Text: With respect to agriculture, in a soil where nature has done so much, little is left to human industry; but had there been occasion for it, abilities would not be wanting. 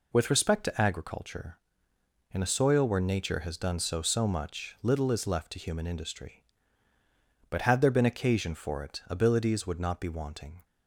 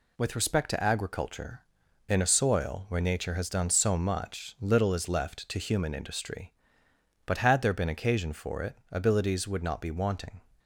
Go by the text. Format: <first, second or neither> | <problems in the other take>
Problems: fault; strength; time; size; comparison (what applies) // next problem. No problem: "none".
second | says "so" twice; at 4.0 s